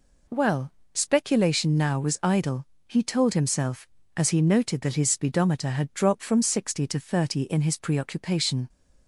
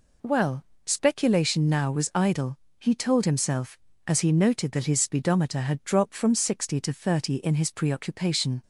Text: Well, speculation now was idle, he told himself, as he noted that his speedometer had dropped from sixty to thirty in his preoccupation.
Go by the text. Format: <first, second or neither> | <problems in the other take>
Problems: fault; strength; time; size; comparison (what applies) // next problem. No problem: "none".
neither | none